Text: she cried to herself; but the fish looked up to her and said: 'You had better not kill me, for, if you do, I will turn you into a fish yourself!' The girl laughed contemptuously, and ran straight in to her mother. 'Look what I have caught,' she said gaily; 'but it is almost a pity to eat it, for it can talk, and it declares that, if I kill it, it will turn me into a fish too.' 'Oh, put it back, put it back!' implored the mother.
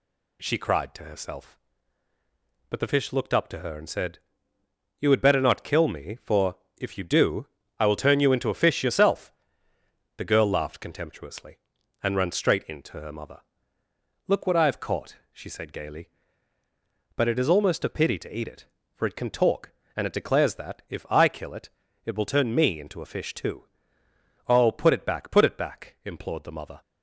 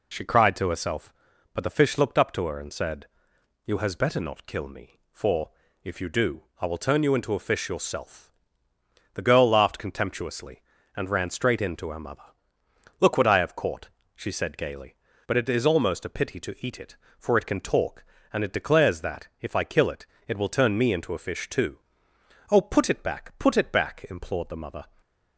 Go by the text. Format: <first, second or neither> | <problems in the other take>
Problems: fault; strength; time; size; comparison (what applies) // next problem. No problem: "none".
first | says "has" for "had"; at 3.7 s // stays silent after the last word; slight; from 24.8 s on; 0.5 s long